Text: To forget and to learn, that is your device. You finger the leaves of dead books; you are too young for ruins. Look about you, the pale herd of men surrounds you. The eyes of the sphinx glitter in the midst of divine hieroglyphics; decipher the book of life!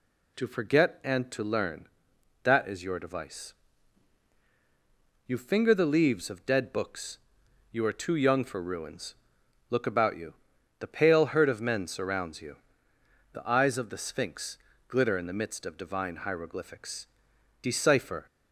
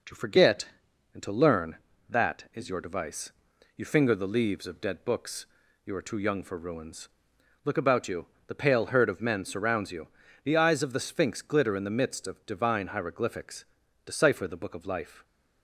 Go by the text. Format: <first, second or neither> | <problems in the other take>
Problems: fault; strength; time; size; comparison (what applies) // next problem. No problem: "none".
second | pauses between "sphinx" and "glitter"; slight; at 14.5 s; 0.30 s long // stops before "the book of life"; at 18.2 s